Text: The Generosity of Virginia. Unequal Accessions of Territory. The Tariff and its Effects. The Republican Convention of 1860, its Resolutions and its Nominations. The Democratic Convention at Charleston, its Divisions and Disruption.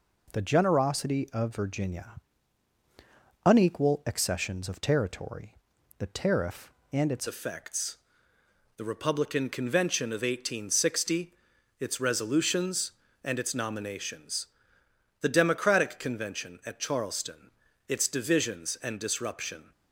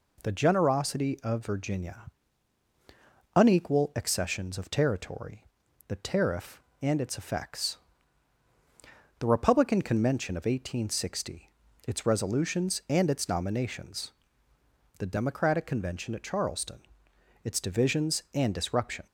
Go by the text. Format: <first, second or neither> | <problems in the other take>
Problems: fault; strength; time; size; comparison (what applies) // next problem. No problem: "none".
second | changes voice at "Effects"; from 7.2 s on; 12.5 s long